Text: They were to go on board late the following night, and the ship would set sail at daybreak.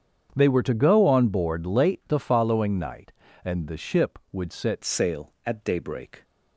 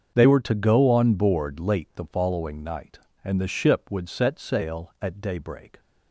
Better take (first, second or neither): second